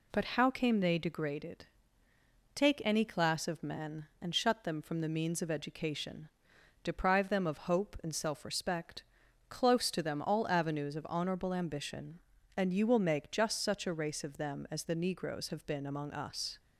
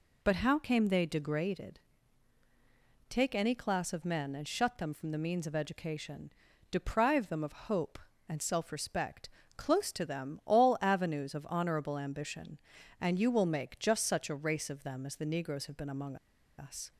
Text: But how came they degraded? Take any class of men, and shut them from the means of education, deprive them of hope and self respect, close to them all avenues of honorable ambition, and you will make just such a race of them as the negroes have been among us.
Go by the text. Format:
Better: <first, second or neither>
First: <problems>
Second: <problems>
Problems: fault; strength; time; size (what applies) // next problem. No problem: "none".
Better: first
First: none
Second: pauses between "among" and "us"; at 16.1 s; 0.42 s long